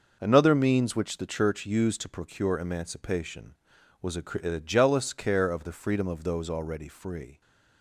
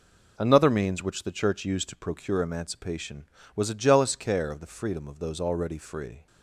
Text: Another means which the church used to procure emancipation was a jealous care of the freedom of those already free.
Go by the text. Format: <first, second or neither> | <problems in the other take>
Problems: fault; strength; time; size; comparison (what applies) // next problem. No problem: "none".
second | says "a" twice; at 4.4 s